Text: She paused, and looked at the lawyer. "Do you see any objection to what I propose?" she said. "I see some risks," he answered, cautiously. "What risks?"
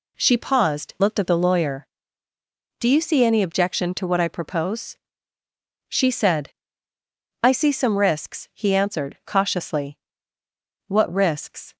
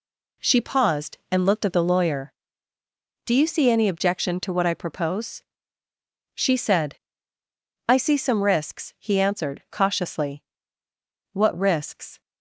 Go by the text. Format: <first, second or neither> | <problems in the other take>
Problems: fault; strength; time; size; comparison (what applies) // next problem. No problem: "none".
second | skips "and"; at 0.9 s